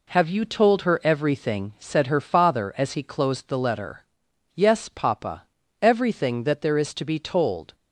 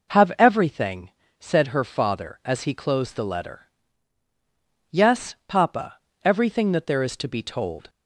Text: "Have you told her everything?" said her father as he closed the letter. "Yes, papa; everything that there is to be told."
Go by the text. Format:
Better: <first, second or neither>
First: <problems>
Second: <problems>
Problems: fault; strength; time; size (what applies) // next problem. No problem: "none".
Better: first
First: none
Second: skips "you told her"; at 0.3 s